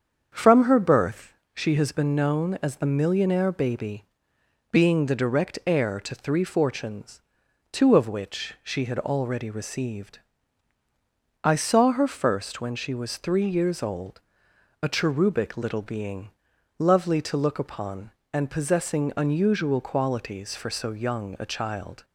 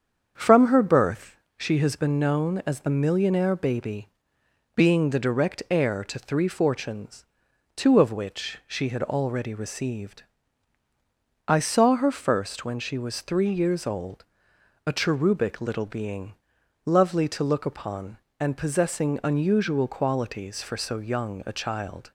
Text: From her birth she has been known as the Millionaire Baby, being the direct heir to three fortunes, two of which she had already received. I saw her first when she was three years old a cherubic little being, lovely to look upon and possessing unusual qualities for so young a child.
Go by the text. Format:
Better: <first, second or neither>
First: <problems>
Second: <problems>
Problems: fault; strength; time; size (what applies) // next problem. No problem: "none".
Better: neither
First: starts louder than the rest; strong; until 1.5 s; 7.5 dB // pauses between "birth" and "she"; slight; at 1.3 s; 0.22 s long // pauses between "old" and "a"; noticeable; at 14.2 s; 0.62 s long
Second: starts louder than the rest; strong; until 1.5 s; 7.5 dB // pauses between "birth" and "she"; slight; at 1.3 s; 0.22 s long // pauses between "old" and "a"; noticeable; at 14.2 s; 0.62 s long